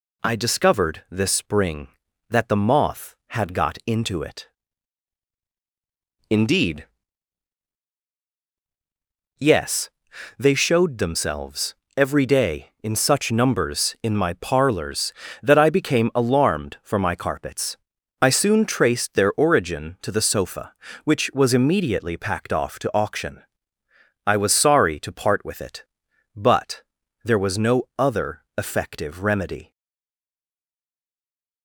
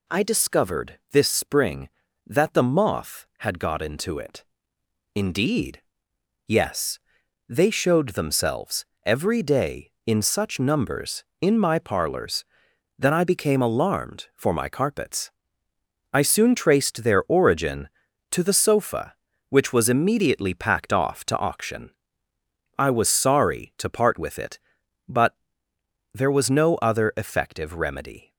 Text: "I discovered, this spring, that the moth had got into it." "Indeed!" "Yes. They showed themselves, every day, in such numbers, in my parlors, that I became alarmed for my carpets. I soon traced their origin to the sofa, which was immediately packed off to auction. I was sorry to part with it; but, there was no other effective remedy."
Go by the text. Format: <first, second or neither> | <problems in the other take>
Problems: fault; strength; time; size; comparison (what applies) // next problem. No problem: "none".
second | stays silent after the last word; noticeable; from 29.7 s on; 1.9 s long